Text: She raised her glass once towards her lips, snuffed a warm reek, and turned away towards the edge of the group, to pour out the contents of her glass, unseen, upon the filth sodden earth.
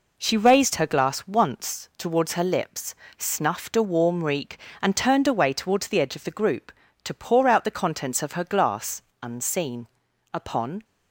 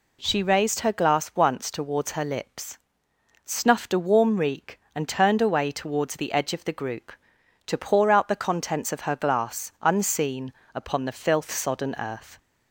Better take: second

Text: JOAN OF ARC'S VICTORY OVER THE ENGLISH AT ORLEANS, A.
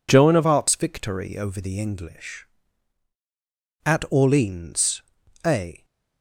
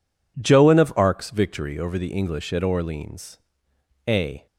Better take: second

